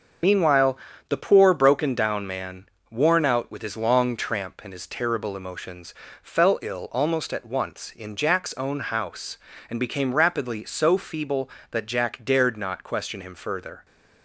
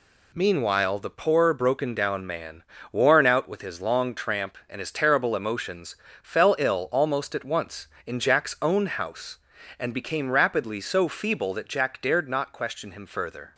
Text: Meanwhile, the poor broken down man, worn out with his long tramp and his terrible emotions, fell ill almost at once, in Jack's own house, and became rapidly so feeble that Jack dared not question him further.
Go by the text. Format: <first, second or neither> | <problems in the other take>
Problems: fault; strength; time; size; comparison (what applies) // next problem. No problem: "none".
second | loses the start of "Meanwhile"; at 0.2 s; 40 ms // starts louder than the rest; until 1.5 s; 6.5 dB